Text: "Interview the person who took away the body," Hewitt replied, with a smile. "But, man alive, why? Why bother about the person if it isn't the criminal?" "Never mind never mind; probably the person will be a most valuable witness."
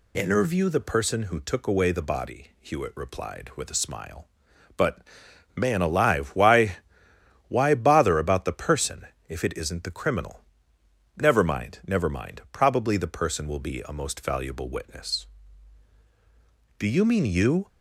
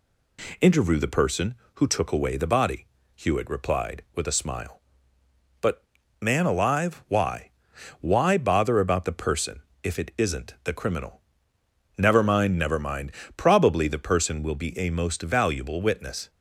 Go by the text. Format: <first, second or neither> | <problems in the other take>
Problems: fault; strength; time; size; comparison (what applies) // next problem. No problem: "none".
second | pauses between "person" and "if"; slight; at 9.0 s; 0.22 s long; slight in the second // goes on to say "Do you mean you"; noticeable; from 16.7 s on; 0.90 s long